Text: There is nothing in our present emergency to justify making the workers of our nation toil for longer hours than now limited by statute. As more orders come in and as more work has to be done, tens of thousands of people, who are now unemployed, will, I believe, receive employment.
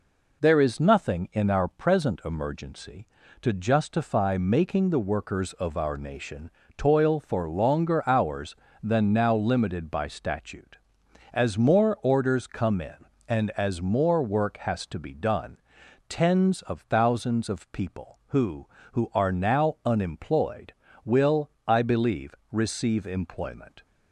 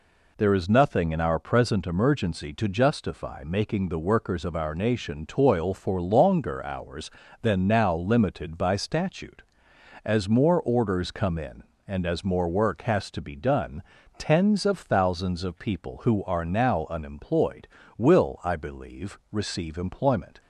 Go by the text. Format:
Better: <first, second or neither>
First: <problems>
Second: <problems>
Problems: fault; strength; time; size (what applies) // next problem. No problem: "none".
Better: second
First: pauses between "nation" and "toil"; slight; at 6.5 s; 0.26 s long // says "who" twice; at 18.9 s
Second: none